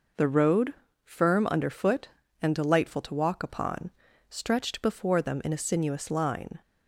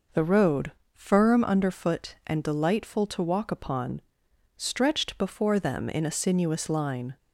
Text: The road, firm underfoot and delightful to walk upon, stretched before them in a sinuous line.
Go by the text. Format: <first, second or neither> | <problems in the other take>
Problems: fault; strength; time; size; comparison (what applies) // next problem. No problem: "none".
neither | none